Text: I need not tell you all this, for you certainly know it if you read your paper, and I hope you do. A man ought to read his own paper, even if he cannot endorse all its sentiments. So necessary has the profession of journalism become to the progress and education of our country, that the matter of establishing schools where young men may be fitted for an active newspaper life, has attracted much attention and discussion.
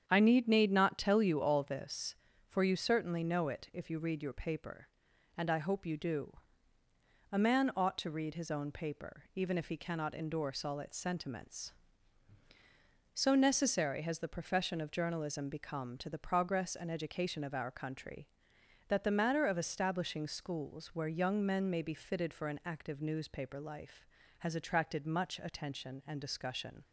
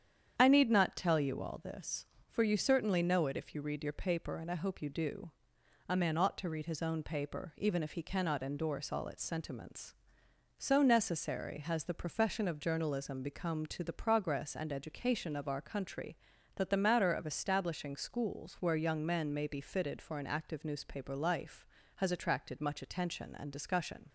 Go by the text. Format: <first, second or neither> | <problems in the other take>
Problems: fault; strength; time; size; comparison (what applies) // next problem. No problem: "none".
second | starts louder than the rest; strong; until 1.0 s; 8 dB; strong in the second // says "need" twice; at 0.4 s